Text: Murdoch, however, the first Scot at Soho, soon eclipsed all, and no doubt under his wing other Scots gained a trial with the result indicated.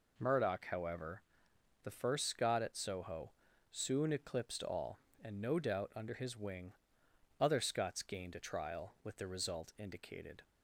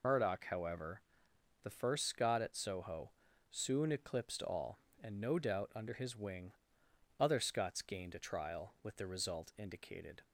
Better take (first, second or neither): first